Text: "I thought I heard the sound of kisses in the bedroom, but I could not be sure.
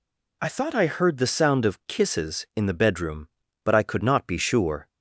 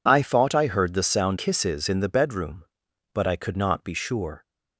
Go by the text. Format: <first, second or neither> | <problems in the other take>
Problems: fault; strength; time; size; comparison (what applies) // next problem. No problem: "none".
first | skips "of"; at 1.3 s